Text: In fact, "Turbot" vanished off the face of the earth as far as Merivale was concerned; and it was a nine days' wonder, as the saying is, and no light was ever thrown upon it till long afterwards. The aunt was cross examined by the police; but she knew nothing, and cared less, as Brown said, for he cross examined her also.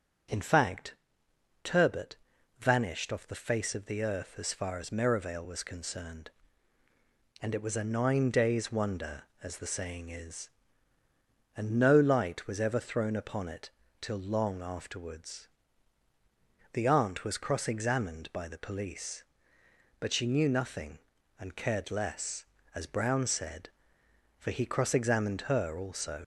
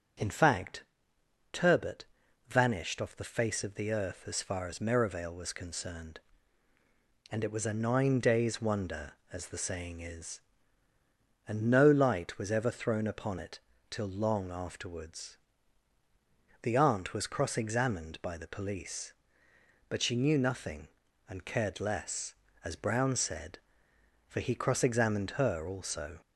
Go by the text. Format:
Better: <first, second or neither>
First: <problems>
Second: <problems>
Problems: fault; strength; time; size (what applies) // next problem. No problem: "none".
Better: second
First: starts louder than the rest; strong; until 2.0 s; 7 dB // pauses between "Turbot" and "vanished"; at 2.1 s; 0.44 s long // pauses between "it" and "till"; slight; at 13.6 s; 0.32 s long // leaves "also" unfinished; at 26.2 s; 65 ms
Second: starts louder than the rest; strong; until 1.8 s; 7.5 dB // pauses between "Turbot" and "vanished"; at 2.0 s; 0.44 s long // pauses between "it" and "till"; slight; at 13.5 s; 0.32 s long